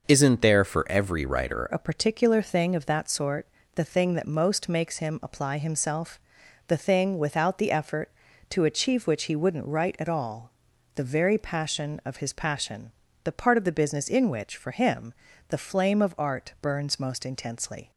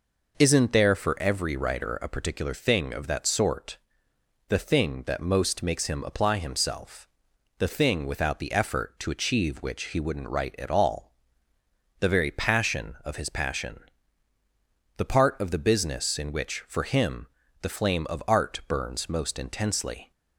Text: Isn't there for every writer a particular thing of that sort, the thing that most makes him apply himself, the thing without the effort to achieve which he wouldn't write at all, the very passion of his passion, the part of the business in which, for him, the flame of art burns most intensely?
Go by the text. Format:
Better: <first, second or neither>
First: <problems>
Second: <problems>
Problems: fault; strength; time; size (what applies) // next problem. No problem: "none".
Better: second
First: changes voice at "a"; from 1.6 s on; 16.3 s long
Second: none